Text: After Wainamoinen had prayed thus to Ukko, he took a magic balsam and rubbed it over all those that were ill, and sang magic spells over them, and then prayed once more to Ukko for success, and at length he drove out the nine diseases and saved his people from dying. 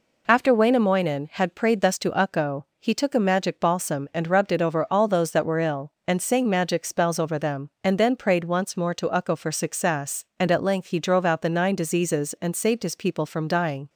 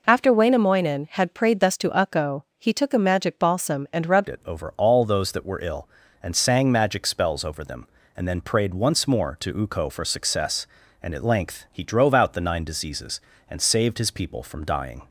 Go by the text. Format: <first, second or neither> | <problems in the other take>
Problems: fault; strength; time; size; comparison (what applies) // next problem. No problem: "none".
first | changes voice at "it"; from 4.2 s on; 10.8 s long